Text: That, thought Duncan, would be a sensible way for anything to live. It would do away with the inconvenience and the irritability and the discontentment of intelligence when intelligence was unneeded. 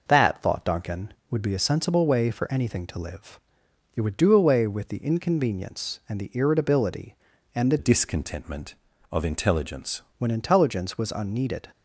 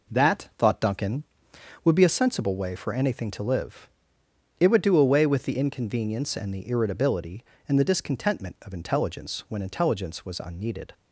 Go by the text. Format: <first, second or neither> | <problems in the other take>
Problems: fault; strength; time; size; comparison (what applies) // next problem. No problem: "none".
second | changes voice from "discontentment" to "intelligence"; from 7.7 to 10.0 s; 2.3 s long